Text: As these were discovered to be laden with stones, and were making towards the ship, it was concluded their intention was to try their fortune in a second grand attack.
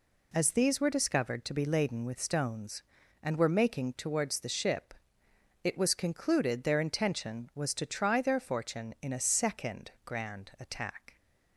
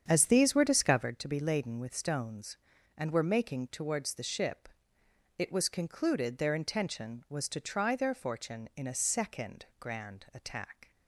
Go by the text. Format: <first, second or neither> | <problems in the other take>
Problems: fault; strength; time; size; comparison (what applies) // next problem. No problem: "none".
first | starts louder than the rest; strong; until 1.1 s; 8 dB // pauses between "second" and "grand"; slight; at 9.6 s; 0.16 s long; slight in the first